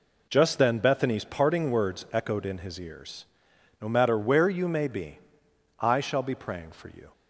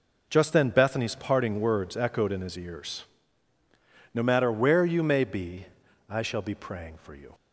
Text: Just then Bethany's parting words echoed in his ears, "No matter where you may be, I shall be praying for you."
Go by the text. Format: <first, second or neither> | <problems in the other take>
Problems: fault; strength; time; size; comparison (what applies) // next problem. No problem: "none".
neither | none